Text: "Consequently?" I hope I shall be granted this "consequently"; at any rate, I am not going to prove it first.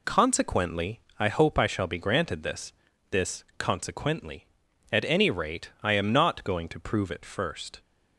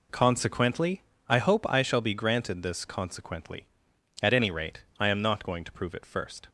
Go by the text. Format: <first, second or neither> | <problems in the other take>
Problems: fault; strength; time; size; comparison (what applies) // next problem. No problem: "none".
second | says "this" twice; at 3.0 s